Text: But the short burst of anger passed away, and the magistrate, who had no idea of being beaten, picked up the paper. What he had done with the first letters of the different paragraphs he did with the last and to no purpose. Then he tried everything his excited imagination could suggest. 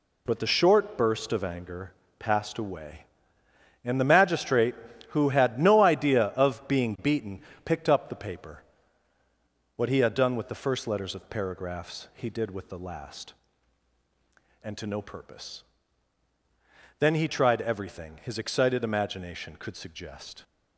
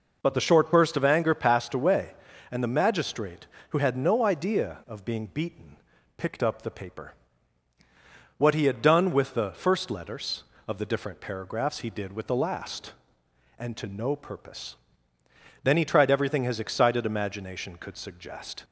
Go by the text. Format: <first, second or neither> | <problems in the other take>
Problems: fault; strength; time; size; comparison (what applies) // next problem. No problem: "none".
second | pauses between "anger" and "passed"; slight; at 1.9 s; 0.26 s long // skips "the different"; at 11.3 s